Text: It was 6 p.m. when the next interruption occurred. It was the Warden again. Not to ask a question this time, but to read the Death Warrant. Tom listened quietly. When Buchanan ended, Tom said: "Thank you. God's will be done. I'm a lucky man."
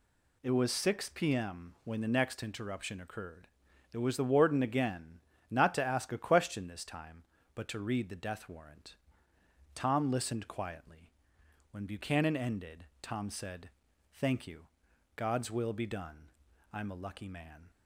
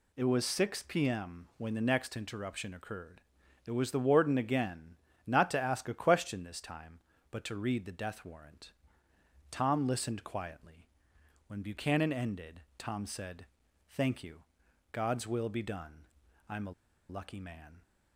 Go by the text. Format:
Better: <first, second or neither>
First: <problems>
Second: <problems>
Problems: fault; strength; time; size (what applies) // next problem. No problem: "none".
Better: first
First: none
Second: pauses between "a" and "lucky"; at 16.7 s; 0.37 s long